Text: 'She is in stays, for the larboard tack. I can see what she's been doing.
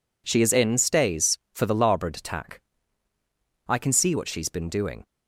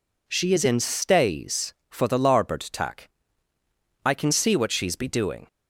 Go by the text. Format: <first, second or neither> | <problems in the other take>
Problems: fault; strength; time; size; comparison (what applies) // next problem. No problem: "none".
first | says "be" for "been"; at 4.9 s